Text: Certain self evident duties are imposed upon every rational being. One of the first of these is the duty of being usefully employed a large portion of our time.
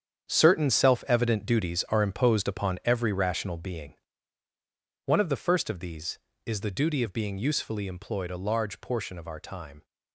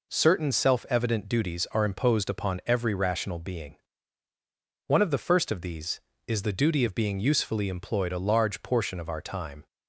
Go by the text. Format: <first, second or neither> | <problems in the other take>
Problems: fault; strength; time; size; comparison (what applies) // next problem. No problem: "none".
second | gets quieter; strong; throughout; 11.5 dB